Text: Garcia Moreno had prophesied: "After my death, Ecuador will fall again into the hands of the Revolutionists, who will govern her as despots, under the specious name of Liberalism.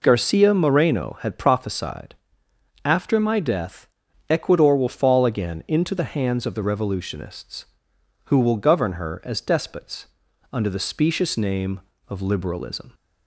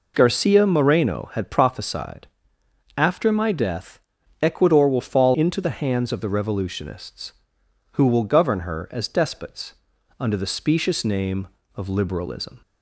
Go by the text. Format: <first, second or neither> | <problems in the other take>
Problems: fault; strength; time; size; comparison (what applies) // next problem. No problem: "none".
first | skips "again"; at 5.3 s